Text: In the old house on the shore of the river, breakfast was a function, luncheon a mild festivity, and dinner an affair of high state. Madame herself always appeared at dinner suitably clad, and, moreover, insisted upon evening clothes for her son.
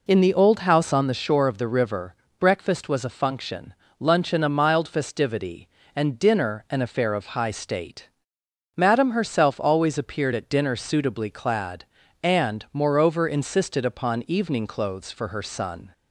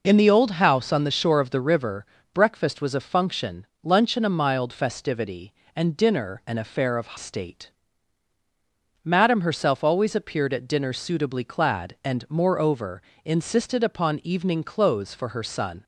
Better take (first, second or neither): first